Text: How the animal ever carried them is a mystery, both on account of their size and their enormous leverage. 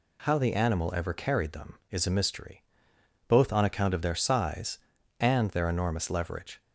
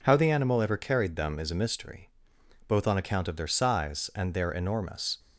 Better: first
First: none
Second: stops before "leverage"; at 5.1 s

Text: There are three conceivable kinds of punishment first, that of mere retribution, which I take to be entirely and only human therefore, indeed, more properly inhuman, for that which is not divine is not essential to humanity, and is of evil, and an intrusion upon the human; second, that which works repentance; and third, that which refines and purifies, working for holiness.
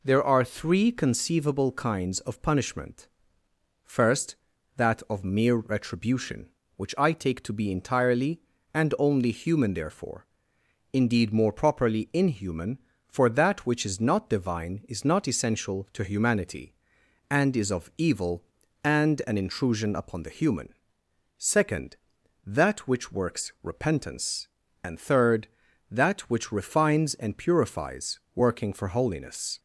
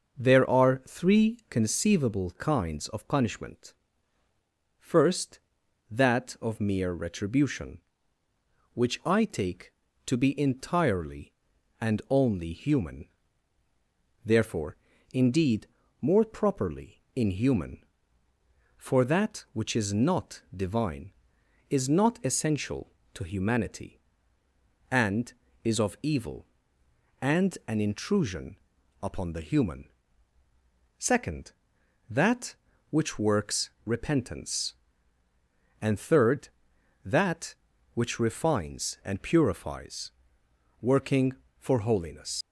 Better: first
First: pauses between "punishment" and "first"; noticeable; at 3.0 s; 0.78 s long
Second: starts louder than the rest; until 1.2 s; 6.5 dB // pauses between "punishment" and "first"; at 3.7 s; 1.0 s long // pauses between "human" and "therefore"; at 13.0 s; 1.1 s long // pauses between "not" and "divine"; slight; at 20.4 s; 0.16 s long // pauses between "intrusion" and "upon"; at 28.5 s; 0.44 s long // leaves "holiness" unfinished; at 42.4 s; 90 ms

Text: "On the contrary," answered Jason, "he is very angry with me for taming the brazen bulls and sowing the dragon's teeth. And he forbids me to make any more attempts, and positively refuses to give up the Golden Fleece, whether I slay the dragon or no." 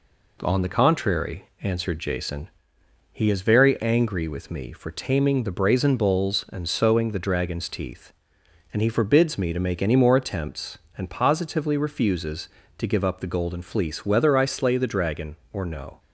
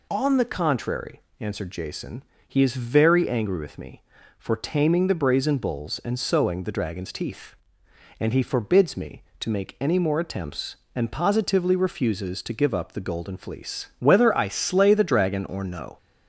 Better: neither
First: none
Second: none

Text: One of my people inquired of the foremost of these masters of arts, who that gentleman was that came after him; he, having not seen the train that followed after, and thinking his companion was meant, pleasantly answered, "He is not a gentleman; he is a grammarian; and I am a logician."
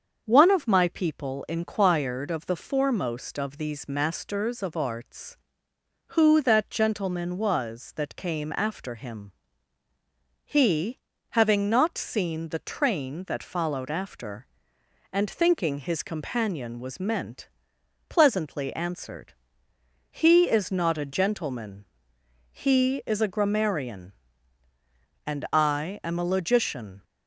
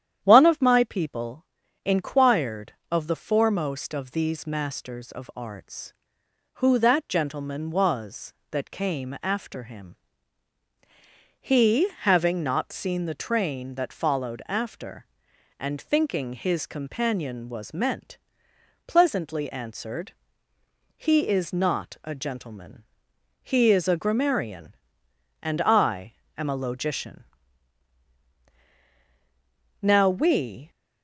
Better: first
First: starts louder than the rest; until 1.2 s; 7 dB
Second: starts louder than the rest; strong; until 1.2 s; 10 dB // pauses between "people" and "inquired"; at 1.4 s; 0.38 s long // pauses between "I" and "am"; slight; at 26.1 s; 0.24 s long // goes on to say "Now we"; noticeable; from 29.8 s on; 0.86 s long

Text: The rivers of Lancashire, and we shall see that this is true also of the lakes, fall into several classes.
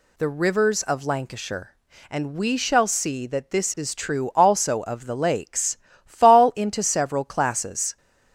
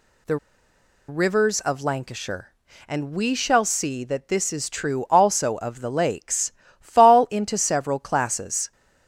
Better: first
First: none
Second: pauses between "The" and "rivers"; noticeable; at 0.3 s; 0.72 s long

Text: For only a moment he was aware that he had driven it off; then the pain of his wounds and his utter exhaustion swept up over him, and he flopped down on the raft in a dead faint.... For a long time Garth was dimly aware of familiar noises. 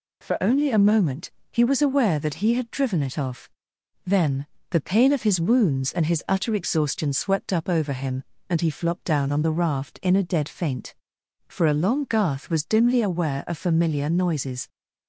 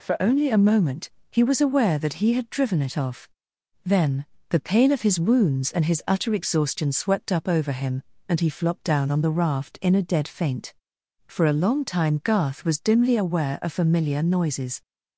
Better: second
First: pauses between "moment" and "he"; slight; at 1.3 s; 0.18 s long // pauses between "then" and "the"; slight; at 4.4 s; 0.24 s long // skips "time"; at 12.0 s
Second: pauses between "moment" and "he"; slight; at 1.1 s; 0.18 s long // pauses between "then" and "the"; slight; at 4.2 s; 0.24 s long

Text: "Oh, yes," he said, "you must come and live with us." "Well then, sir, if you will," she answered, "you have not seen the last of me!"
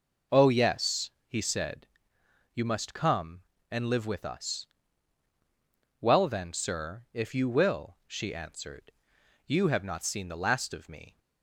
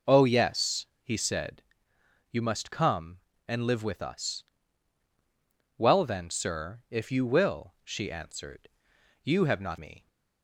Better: first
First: none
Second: skips "seen the last of"; at 9.7 s

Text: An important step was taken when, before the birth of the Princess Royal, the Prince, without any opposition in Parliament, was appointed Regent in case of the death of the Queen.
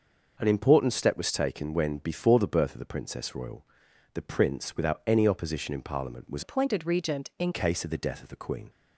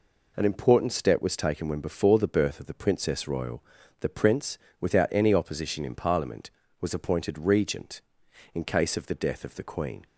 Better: second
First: changes voice from "appointed" to "in"; from 6.4 to 7.5 s; 1.1 s long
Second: none

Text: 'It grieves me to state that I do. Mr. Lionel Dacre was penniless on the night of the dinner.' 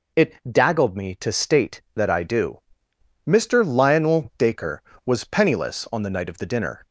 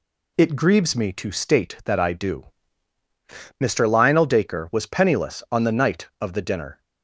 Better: second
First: says "daggled" for "grieves"; at 0.4 s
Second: none

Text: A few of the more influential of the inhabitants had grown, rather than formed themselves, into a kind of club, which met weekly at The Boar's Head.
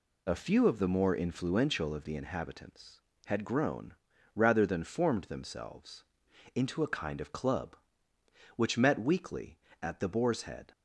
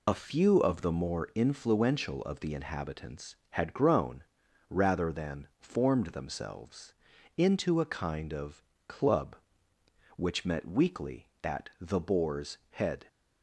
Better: first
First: none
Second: loses the start of "A"; at 0.0 s; 60 ms // pauses between "of" and "club"; slight; at 8.6 s; 0.24 s long // pauses between "Boar's" and "Head"; slight; at 12.5 s; 0.16 s long

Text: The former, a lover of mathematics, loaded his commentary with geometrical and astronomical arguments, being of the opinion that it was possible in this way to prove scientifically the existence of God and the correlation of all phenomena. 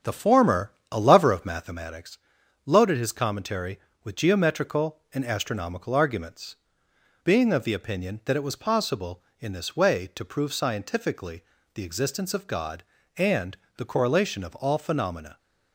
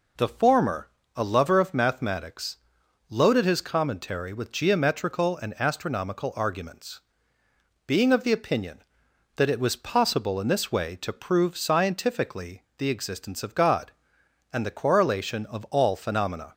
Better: second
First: starts louder than the rest; strong; until 1.8 s; 8 dB // pauses between "scientifically" and "the"; slight; at 11.4 s; 0.32 s long // pauses between "and" and "the"; slight; at 13.5 s; 0.22 s long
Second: pauses between "scientifically" and "the"; slight; at 12.6 s; 0.16 s long

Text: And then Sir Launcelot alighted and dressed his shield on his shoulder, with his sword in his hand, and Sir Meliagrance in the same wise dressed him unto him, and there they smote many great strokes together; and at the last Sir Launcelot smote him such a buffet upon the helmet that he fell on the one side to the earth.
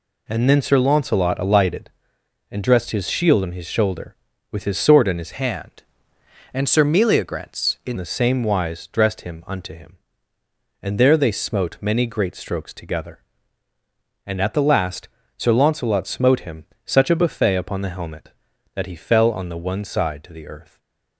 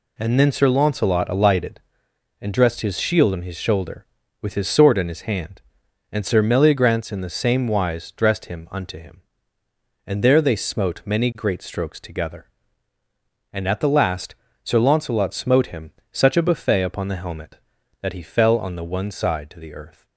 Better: second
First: changes voice from "hand" to "in"; from 5.3 to 7.9 s; 2.6 s long // pauses between "last" and "Sir"; slight; at 15.0 s; 0.30 s long // pauses between "him" and "such"; slight; at 16.6 s; 0.18 s long // stays silent after the last word; slight; from 20.6 s on; 0.5 s long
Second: pauses between "last" and "Sir"; slight; at 14.3 s; 0.30 s long // pauses between "him" and "such"; slight; at 15.9 s; 0.18 s long

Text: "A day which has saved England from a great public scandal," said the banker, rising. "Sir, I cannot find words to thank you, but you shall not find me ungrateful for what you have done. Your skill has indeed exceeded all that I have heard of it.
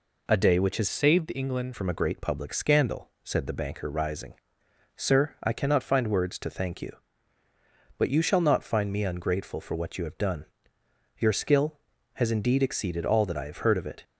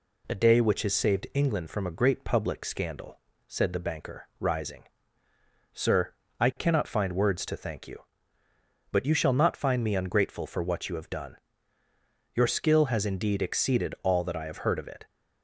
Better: second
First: changes voice from "saved" to "England"; from 0.9 to 1.7 s; 0.8 s long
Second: none

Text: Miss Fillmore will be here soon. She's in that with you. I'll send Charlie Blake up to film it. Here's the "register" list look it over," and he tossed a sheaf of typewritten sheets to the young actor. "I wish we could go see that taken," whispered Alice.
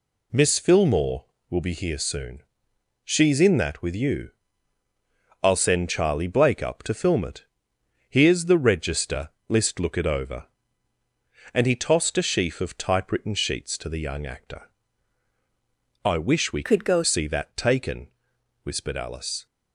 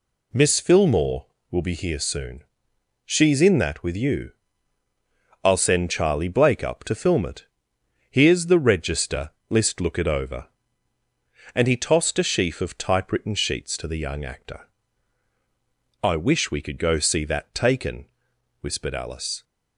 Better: second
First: pauses between "register" and "list"; slight; at 9.2 s; 0.20 s long // changes voice from "could" to "go"; from 16.6 to 17.0 s; 0.4 s long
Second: pauses between "register" and "list"; slight; at 9.2 s; 0.20 s long

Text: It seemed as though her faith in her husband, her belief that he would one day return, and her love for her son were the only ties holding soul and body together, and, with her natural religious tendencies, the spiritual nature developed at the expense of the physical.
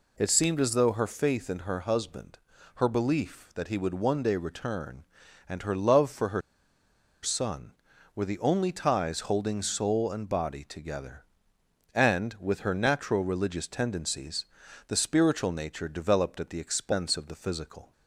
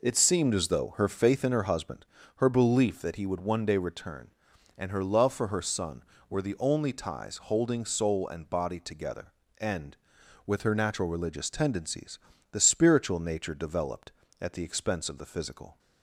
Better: second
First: pauses between "her" and "son"; noticeable; at 6.4 s; 0.82 s long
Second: none

